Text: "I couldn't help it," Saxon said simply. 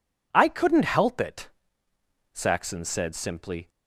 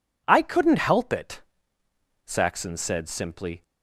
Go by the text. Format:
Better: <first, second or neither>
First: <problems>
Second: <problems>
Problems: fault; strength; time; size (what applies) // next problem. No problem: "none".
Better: neither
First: none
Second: none